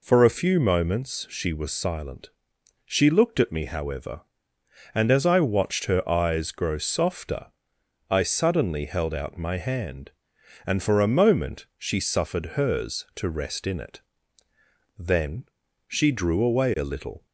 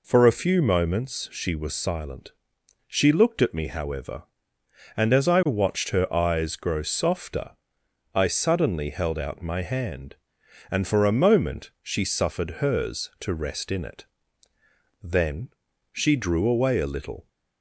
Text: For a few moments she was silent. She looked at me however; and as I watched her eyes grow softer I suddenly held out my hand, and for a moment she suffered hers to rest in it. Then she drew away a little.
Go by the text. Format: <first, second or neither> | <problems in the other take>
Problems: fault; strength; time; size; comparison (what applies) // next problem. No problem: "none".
neither | pauses between "softer" and "I"; noticeable; the same in both // pauses between "Then" and "she"; the same in both